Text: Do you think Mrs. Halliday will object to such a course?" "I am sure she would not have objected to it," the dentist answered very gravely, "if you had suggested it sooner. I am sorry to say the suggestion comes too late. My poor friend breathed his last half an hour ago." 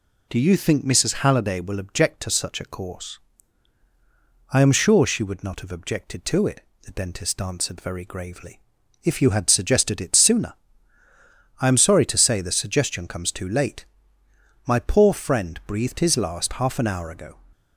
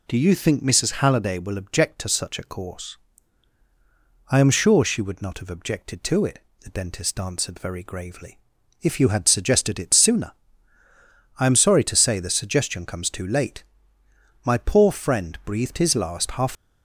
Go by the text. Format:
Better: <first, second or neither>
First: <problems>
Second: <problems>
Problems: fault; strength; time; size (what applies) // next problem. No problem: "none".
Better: first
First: none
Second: stops before "an hour ago"; at 16.5 s